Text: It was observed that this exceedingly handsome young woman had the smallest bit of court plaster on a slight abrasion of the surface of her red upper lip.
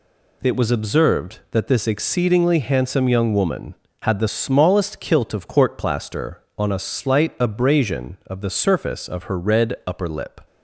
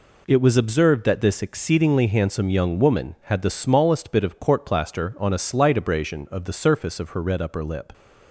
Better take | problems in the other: second | says "kilt" for "bit"; at 5.0 s

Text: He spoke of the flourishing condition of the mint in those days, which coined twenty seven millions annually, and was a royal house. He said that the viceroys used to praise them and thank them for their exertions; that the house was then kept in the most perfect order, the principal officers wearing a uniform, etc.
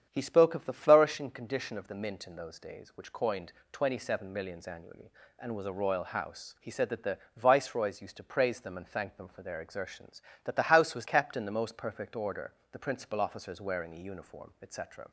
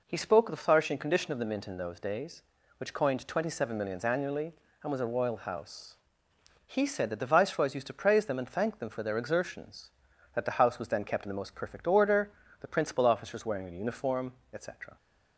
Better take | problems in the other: second | starts louder than the rest; strong; until 1.1 s; 8.5 dB // pauses between "coined" and "twenty"; slight; at 3.5 s; 0.20 s long // pauses between "the" and "viceroys"; slight; at 7.1 s; 0.18 s long // skips "then"; at 11.0 s

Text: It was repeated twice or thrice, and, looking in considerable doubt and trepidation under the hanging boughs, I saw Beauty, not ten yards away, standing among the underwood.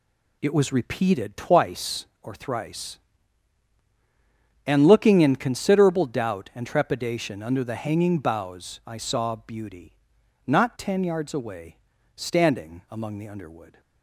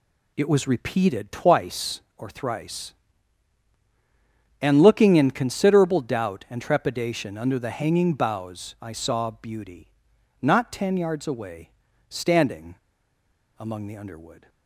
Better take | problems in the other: first | pauses between "standing" and "among"; noticeable; at 12.7 s; 0.83 s long

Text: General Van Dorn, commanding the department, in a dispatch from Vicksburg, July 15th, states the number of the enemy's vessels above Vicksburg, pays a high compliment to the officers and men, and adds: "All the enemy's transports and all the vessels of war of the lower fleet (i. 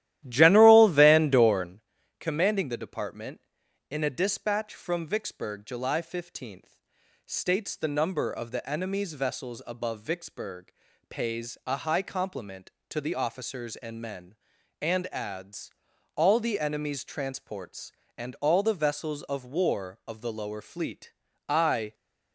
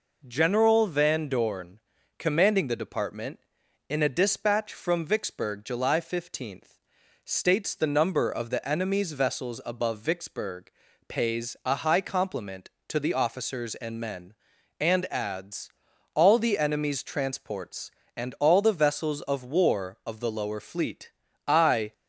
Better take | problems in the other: second | starts louder than the rest; strong; until 1.9 s; 13.5 dB

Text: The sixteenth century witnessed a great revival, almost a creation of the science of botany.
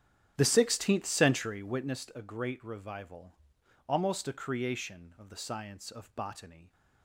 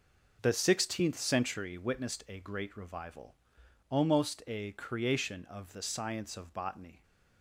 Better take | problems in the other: second | starts louder than the rest; strong; until 1.9 s; 10 dB

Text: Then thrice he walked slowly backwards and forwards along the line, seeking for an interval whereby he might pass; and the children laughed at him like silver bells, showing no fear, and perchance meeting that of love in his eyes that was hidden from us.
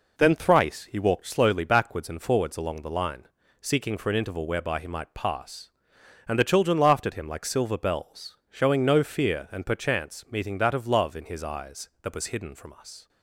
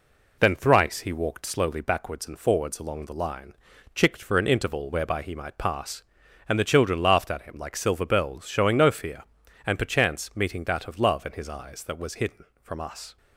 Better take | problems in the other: first | says "chicked" for "seeking"; at 3.9 s

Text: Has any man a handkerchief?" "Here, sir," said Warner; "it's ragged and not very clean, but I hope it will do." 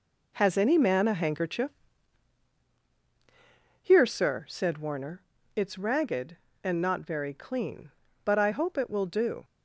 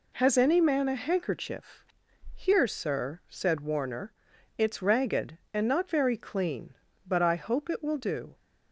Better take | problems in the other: second | gets quieter; strong; throughout; 8.5 dB

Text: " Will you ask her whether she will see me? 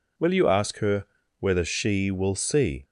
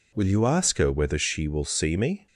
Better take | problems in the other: second | pauses between "her" and "whether"; slight; at 1.0 s; 0.34 s long // stops before "me"; at 2.8 s

